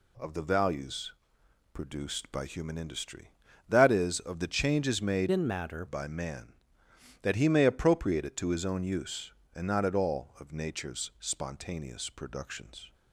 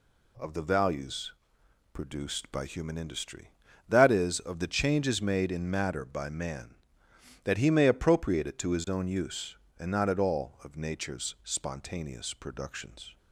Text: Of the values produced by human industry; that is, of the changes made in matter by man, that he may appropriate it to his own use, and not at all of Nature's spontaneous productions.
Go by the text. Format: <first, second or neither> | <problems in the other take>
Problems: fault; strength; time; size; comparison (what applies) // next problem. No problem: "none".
second | pauses between "values" and "produced"; noticeable; at 1.1 s; 0.62 s long; noticeable in the second // changes voice from "in" to "matter"; from 5.3 to 5.8 s; 0.5 s long